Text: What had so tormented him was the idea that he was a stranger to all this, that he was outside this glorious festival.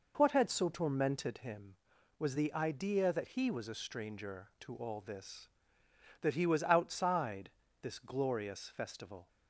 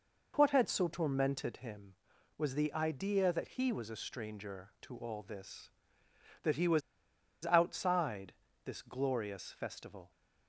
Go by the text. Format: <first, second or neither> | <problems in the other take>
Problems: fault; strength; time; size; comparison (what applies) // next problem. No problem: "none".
first | pauses between "was" and "outside"; noticeable; at 6.8 s; 0.63 s long // pauses between "outside" and "this"; slight; at 8.3 s; 0.32 s long; slight in the first